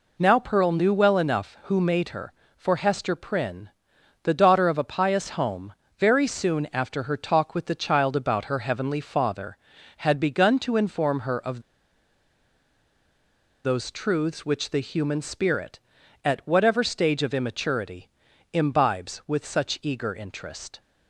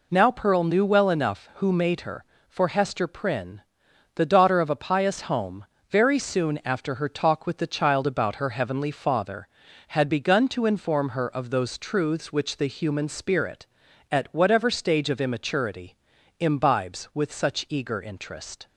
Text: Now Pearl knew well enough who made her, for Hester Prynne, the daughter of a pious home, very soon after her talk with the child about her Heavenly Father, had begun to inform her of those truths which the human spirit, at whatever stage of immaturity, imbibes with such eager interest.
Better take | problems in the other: second | pauses between "of" and "those"; strong; at 11.6 s; 2.0 s long

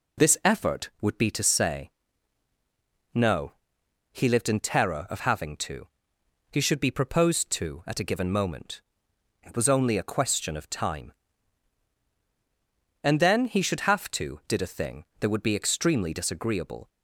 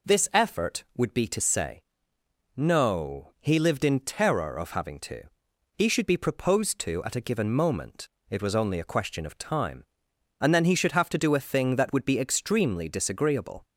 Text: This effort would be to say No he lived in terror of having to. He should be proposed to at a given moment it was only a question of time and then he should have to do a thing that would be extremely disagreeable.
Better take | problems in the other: second | pauses between "say" and "No"; at 1.9 s; 1.2 s long; noticeable in the second // pauses between "No" and "he"; noticeable; at 3.5 s; 0.58 s long // pauses between "moment" and "it"; noticeable; at 8.8 s; 0.62 s long; slight in the second // says "did" for "do"; at 14.4 s

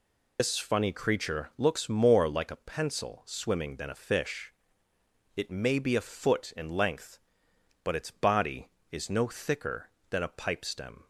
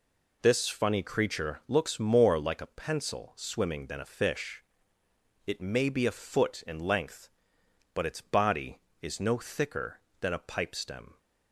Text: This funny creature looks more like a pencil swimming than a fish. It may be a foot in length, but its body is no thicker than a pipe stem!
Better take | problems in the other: second | loses the start of "This"; at 0.3 s; 85 ms

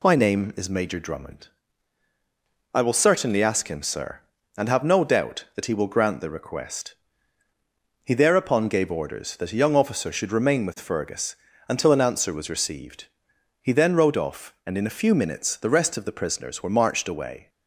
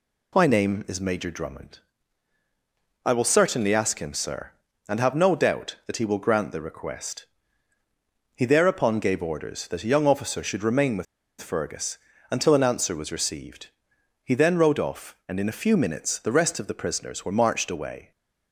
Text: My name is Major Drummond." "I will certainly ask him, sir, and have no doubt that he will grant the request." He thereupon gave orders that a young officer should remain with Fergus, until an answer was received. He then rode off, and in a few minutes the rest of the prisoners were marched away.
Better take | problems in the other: first | pauses between "with" and "Fergus"; slight; at 11.0 s; 0.35 s long

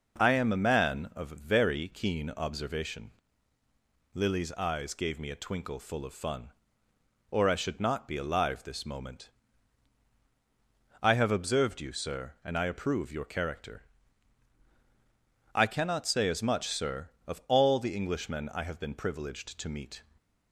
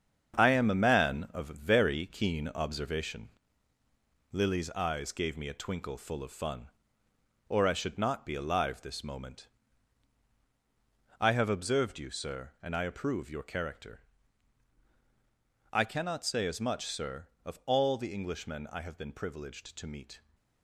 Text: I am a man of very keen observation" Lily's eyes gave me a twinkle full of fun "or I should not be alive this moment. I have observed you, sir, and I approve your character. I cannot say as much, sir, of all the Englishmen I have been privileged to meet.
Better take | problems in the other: first | gets quieter; throughout; 7 dB // pauses between "observation" and "Lily's"; at 3.2 s; 1.0 s long; also in the first

